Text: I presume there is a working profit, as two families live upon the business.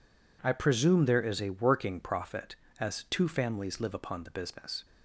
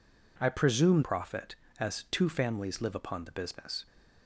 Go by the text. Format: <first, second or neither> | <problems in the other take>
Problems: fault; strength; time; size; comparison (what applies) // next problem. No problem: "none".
first | skips "there is a working"; at 1.0 s